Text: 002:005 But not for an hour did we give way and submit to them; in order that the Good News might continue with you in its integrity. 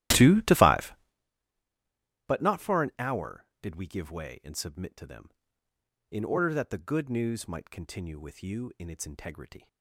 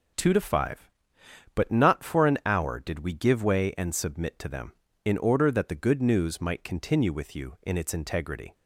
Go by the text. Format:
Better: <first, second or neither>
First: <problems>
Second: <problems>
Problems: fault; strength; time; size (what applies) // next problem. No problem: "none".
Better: second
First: starts louder than the rest; strong; until 1.2 s; 14 dB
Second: none